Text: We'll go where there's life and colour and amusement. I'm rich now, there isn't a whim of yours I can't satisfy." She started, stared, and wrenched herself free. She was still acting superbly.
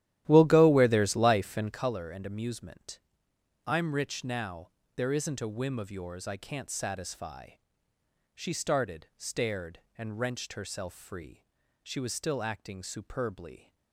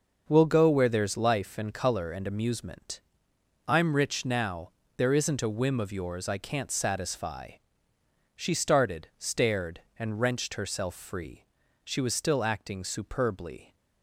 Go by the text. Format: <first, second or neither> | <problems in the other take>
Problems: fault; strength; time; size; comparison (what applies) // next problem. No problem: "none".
second | starts louder than the rest; strong; until 1.8 s; 12.5 dB